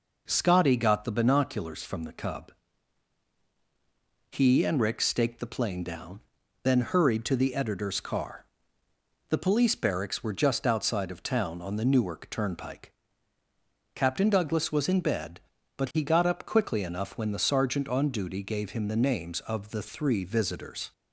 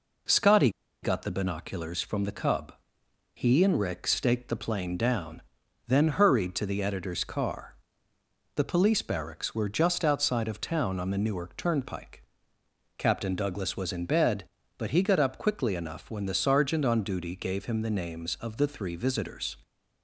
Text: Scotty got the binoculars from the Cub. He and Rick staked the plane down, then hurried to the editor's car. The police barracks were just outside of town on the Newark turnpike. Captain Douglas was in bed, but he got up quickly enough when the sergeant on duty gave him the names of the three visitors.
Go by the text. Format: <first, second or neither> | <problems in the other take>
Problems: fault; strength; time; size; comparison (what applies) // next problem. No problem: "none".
first | pauses between "Scotty" and "got"; slight; at 0.7 s; 0.31 s long